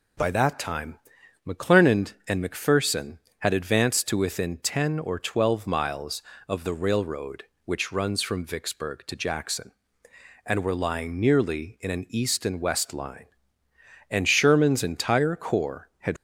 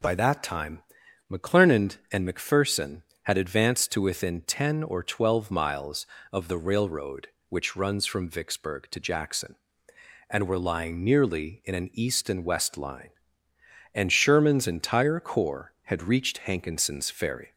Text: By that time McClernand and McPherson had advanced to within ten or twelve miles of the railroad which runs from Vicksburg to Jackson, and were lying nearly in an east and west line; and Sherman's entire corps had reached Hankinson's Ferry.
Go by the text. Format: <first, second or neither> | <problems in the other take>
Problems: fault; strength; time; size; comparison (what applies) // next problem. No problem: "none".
second | pauses between "time" and "McClernand"; noticeable; at 0.9 s; 0.48 s long; noticeable in the second // stops before "reached Hankinson's Ferry"; at 16.1 s